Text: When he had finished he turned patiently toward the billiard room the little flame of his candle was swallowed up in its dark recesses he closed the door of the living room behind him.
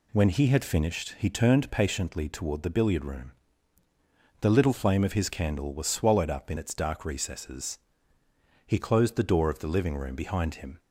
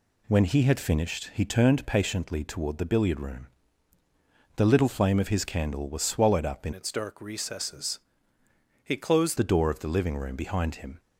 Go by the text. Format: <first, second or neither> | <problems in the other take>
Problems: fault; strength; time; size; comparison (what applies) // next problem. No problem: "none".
first | pauses between "room" and "the"; at 3.4 s; 1.0 s long; also in the first // changes voice from "its" to "closed"; from 6.7 to 9.3 s; 2.6 s long // pauses between "recesses" and "he"; noticeable; at 7.9 s; 0.84 s long; noticeable in the first